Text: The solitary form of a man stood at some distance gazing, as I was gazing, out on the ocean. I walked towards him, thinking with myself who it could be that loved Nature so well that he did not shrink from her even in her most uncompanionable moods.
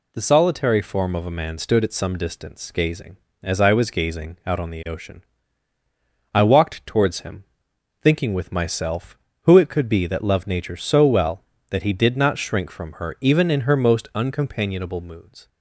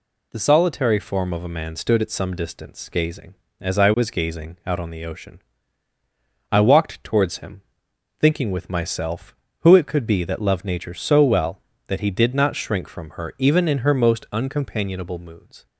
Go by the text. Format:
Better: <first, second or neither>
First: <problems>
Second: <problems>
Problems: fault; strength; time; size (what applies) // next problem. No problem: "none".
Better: neither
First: none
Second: none